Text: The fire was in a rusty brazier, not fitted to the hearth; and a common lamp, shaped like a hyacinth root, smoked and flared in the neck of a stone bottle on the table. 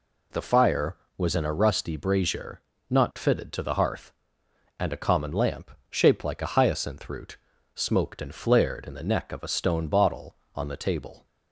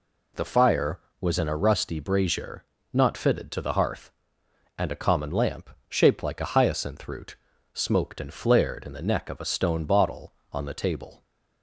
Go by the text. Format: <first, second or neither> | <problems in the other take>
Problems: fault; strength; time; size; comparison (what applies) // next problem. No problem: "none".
neither | none